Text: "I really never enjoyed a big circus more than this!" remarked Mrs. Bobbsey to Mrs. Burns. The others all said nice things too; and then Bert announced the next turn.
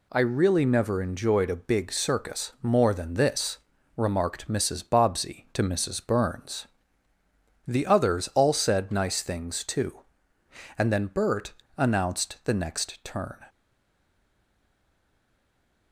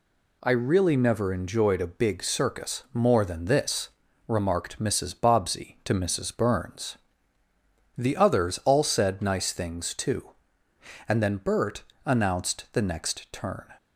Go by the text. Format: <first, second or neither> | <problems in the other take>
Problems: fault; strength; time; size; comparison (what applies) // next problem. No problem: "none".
second | pauses between "Bert" and "announced"; slight; at 11.5 s; 0.24 s long; slight in the second // stays silent after the last word; from 13.4 s on; 2.5 s long